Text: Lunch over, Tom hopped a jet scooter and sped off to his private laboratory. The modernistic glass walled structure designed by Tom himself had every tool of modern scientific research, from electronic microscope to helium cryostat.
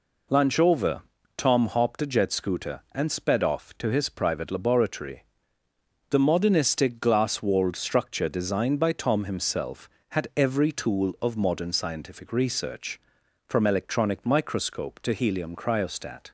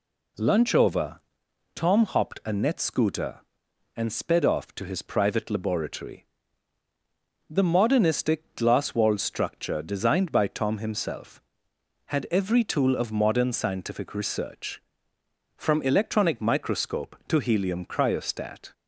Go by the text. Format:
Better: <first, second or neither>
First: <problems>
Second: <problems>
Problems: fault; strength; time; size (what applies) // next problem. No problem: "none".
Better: first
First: none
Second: says "net" for "jet"; at 2.5 s